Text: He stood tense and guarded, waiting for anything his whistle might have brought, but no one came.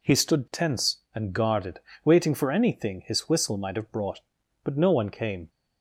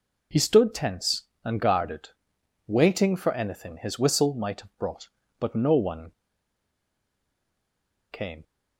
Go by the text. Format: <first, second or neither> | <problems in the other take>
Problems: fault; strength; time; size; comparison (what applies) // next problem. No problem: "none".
first | pauses between "one" and "came"; strong; at 6.1 s; 1.9 s long